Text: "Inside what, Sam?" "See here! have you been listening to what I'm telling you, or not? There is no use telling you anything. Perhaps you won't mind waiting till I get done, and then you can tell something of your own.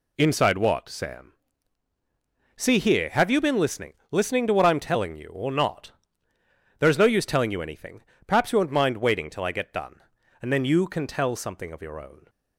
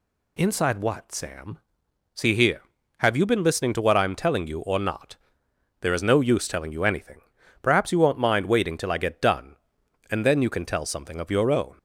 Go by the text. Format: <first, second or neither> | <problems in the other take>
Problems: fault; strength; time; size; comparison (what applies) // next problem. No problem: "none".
second | says "listening" twice; at 4.1 s